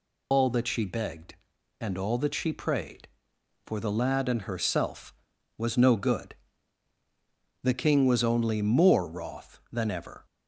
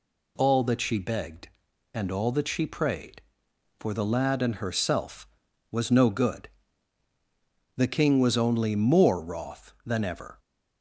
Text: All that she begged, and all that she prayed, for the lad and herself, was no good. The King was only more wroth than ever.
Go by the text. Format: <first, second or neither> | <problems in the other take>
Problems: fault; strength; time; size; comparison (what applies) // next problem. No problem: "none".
second | loses the start of "All"; at 0.3 s; 90 ms